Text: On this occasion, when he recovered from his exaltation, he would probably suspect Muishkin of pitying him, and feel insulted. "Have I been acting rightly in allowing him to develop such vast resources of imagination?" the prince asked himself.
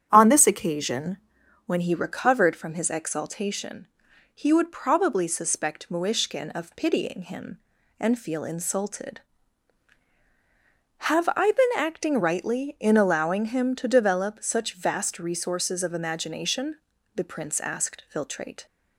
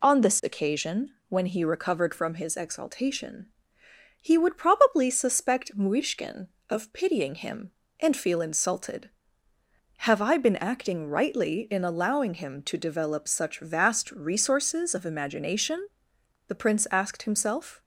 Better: second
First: starts louder than the rest; strong; until 1.1 s; 9 dB // says "filtrate" for "himself"; at 18.1 s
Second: none

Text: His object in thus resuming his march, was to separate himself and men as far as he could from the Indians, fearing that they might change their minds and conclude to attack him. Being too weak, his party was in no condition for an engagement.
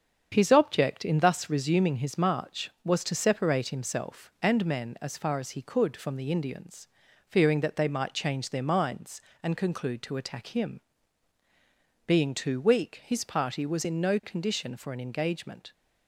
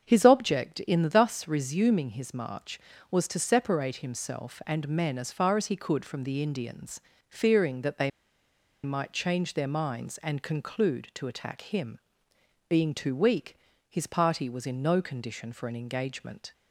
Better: first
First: starts louder than the rest; strong; until 1.3 s; 7.5 dB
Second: starts louder than the rest; strong; until 1.0 s; 7 dB // pauses between "they" and "might"; noticeable; at 8.1 s; 0.74 s long

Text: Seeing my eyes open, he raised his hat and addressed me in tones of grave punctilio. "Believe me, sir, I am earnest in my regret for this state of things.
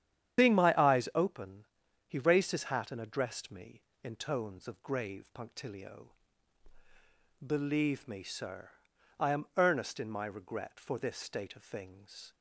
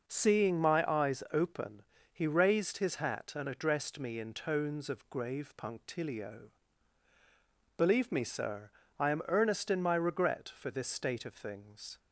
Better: second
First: loses the start of "Seeing"; at 0.3 s; 125 ms // starts louder than the rest; strong; until 1.4 s; 9.5 dB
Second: none

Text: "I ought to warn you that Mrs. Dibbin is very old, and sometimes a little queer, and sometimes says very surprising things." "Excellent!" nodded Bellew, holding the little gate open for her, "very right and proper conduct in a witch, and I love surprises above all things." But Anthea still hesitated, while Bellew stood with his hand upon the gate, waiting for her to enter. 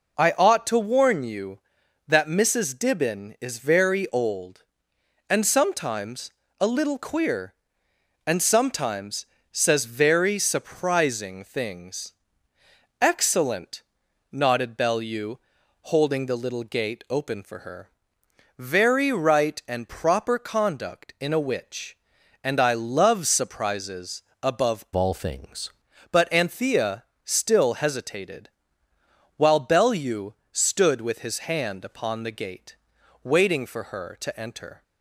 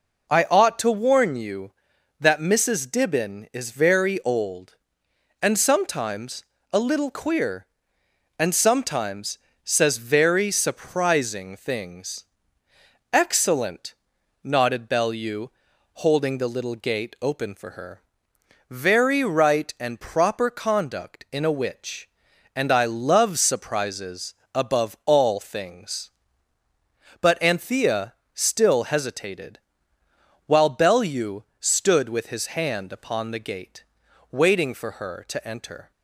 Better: second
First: pauses between "sometimes" and "a"; slight; at 6.3 s; 0.30 s long // pauses between "sometimes" and "says"; slight; at 9.2 s; 0.26 s long // pauses between "surprises" and "above"; slight; at 24.2 s; 0.18 s long // changes voice from "all" to "things"; from 24.9 to 25.7 s; 0.8 s long // pauses between "Anthea" and "still"; slight; at 27.0 s; 0.20 s long // pauses between "Bellew" and "stood"; slight; at 30.3 s; 0.18 s long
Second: pauses between "sometimes" and "a"; slight; at 6.4 s; 0.30 s long // pauses between "sometimes" and "says"; slight; at 9.3 s; 0.26 s long // pauses between "surprises" and "above"; slight; at 24.3 s; 0.18 s long // pauses between "Anthea" and "still"; slight; at 28.1 s; 0.20 s long // pauses between "Bellew" and "stood"; slight; at 31.4 s; 0.16 s long

